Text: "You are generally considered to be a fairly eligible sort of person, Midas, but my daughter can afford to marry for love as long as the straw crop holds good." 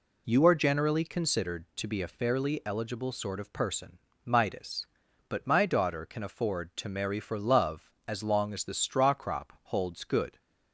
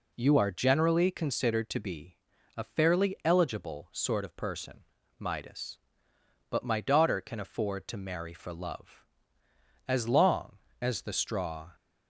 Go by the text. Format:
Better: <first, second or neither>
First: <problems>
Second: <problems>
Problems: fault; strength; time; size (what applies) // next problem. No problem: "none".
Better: first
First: none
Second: pauses between "be" and "a"; at 2.1 s; 0.39 s long // stops before "crop holds good"; at 11.7 s